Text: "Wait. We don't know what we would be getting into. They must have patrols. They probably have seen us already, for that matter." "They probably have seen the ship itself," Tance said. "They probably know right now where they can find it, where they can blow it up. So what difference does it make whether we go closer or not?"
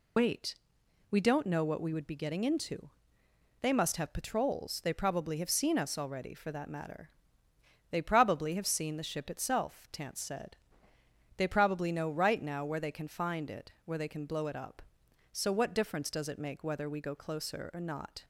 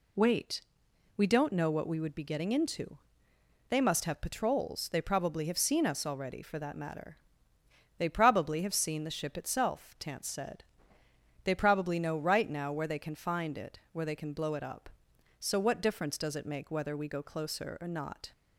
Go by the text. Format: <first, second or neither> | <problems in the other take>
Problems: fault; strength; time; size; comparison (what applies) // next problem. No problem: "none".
second | loses the start of "Wait"; at 0.1 s; 60 ms